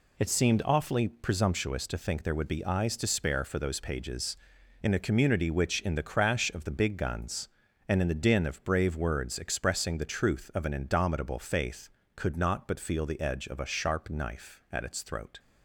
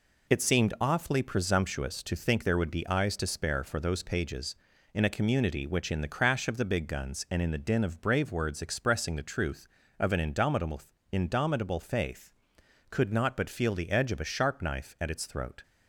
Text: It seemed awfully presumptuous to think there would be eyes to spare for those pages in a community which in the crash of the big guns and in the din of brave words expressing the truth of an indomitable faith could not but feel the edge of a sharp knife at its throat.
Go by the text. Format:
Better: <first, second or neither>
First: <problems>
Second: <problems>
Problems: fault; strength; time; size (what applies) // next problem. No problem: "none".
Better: first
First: none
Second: says "indomitable" twice; at 11.1 s